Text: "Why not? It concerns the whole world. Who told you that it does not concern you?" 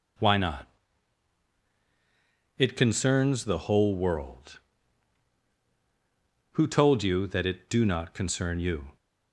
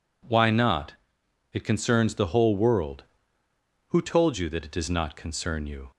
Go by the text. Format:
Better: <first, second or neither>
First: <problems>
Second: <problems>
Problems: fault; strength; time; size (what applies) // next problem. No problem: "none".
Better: second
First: says "do" for "does"; at 7.6 s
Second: none